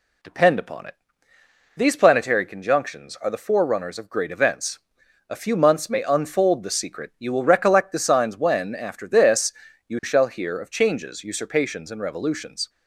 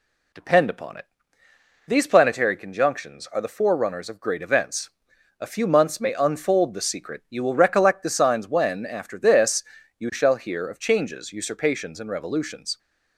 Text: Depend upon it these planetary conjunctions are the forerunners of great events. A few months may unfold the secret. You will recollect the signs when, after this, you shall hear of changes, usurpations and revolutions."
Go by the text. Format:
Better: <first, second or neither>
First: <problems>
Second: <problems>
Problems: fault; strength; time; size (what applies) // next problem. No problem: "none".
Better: neither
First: pauses between "it" and "these"; noticeable; at 0.9 s; 0.82 s long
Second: pauses between "it" and "these"; noticeable; at 1.0 s; 0.82 s long